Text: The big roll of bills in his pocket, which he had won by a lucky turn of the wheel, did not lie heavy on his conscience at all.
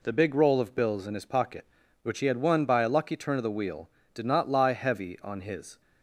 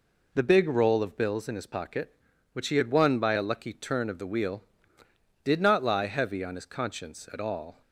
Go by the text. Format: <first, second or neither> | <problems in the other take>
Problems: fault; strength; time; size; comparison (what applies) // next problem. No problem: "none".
second | stops before "conscience at all"; at 5.8 s